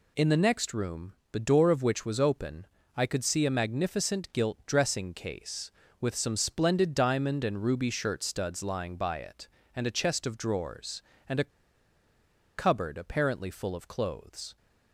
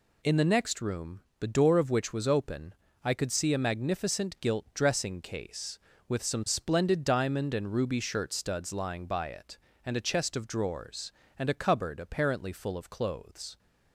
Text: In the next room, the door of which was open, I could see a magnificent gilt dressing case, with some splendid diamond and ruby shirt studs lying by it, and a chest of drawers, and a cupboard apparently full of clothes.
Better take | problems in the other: second | pauses between "a" and "cupboard"; at 11.5 s; 1.0 s long

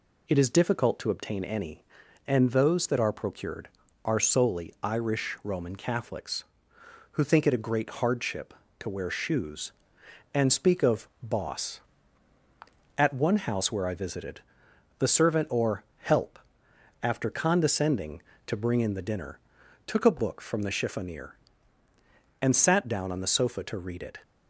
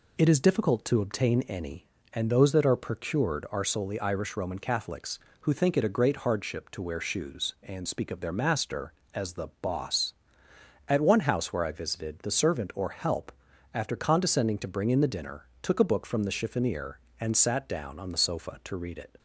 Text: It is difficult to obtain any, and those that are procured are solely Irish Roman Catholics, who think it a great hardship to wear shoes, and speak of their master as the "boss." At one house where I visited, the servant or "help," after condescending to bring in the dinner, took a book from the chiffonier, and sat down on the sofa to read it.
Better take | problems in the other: second | skips "their master as the"; at 11.1 s // pauses between "or" and "help"; slight; at 15.8 s; 0.16 s long

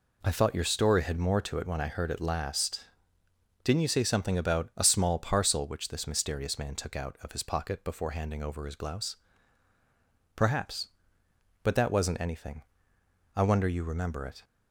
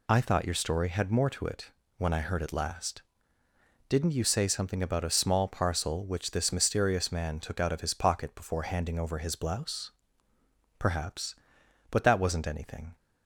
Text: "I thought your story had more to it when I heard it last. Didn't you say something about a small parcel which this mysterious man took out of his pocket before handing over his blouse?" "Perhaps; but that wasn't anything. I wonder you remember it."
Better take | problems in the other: first | pauses between "it" and "when"; slight; at 1.7 s; 0.26 s long // stops before "I wonder you remember it"; at 12.9 s

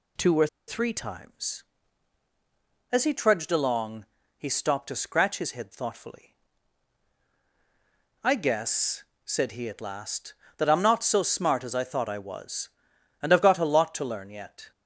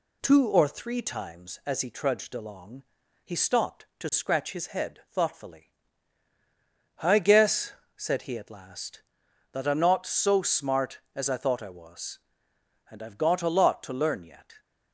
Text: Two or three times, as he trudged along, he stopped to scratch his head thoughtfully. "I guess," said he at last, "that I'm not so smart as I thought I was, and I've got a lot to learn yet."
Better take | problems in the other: second | pauses between "or" and "three"; slight; at 0.4 s; 0.21 s long

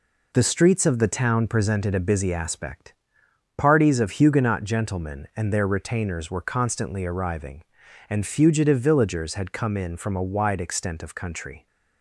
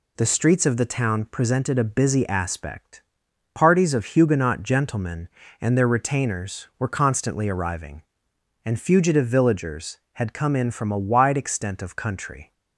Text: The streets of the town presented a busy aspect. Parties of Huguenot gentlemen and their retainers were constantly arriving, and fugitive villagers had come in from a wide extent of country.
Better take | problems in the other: neither | none

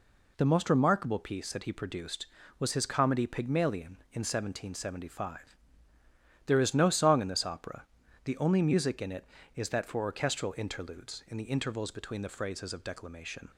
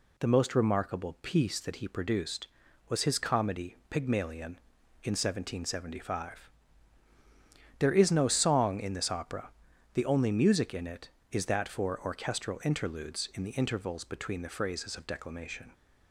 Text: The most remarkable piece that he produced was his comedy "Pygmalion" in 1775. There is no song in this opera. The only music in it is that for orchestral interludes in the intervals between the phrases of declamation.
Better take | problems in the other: neither | none

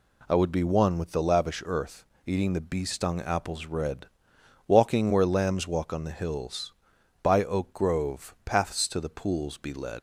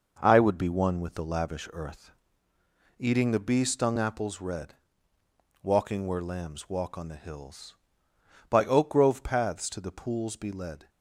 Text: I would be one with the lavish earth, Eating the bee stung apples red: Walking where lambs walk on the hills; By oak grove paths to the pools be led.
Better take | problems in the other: second | leaves "led" unfinished; at 9.9 s; 95 ms

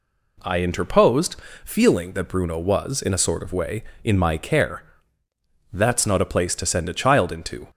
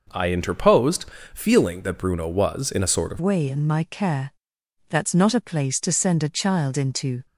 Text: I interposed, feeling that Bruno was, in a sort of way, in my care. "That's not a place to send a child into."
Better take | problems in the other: first | changes voice at "way"; from 3.1 s on; 4.1 s long

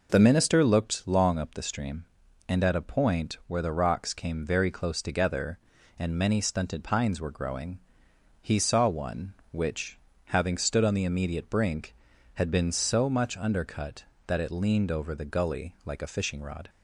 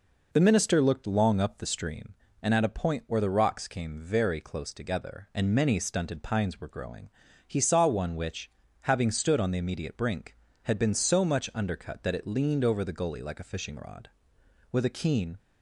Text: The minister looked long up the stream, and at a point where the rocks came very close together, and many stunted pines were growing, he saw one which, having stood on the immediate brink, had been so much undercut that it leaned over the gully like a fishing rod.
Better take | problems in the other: first | goes on to say "With a keen"; noticeable; from 14.7 s on; 0.66 s long

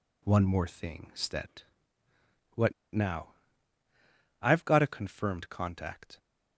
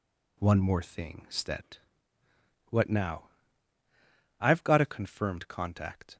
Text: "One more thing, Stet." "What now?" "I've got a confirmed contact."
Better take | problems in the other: second | pauses between "What" and "now"; slight; at 2.7 s; 0.21 s long

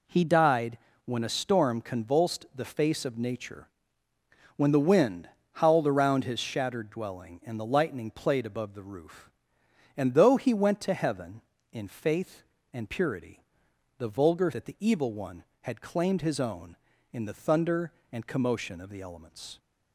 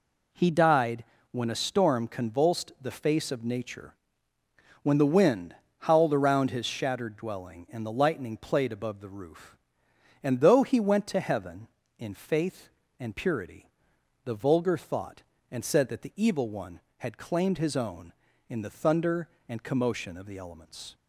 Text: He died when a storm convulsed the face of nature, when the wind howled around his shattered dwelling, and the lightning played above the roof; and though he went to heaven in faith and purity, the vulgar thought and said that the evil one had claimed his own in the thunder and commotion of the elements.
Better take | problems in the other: second | pauses between "died" and "when"; slight; at 0.7 s; 0.28 s long; slight in the second // pauses between "wind" and "howled"; slight; at 5.2 s; 0.24 s long; slight in the second // skips "thought and said"; at 14.5 s

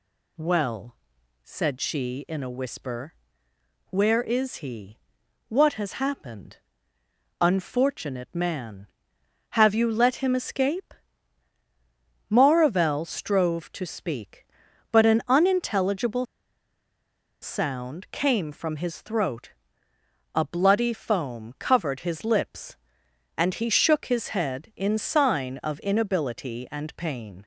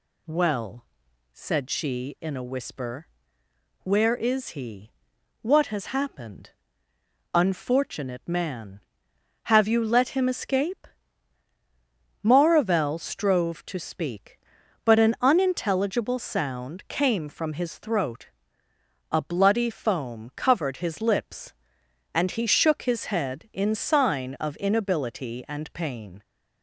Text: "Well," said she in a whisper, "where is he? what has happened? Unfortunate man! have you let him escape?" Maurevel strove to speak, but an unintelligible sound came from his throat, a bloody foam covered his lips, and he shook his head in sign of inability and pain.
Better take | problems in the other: second | pauses between "unintelligible" and "sound"; at 16.2 s; 1.1 s long

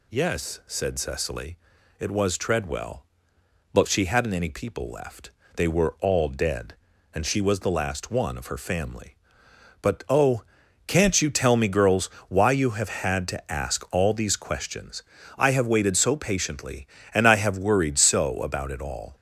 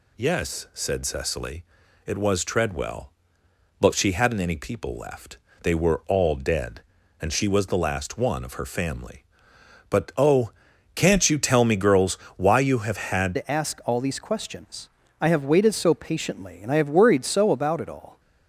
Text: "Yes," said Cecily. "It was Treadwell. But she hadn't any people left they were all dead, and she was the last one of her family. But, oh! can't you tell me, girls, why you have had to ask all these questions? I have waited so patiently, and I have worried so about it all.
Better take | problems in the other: first | pauses between "left" and "they"; slight; at 5.3 s; 0.26 s long; slight in the first // changes voice at "to"; from 13.3 s on; 4.8 s long

